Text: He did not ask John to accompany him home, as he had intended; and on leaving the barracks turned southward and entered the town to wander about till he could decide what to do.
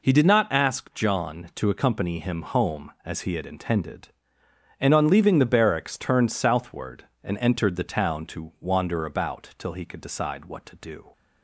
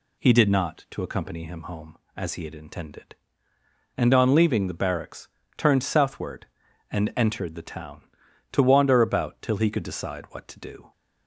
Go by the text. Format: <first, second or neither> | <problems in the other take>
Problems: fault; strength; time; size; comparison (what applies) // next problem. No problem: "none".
first | skips "ask John"; at 0.8 s // pauses between "barracks" and "turned"; slight; at 5.2 s; 0.26 s long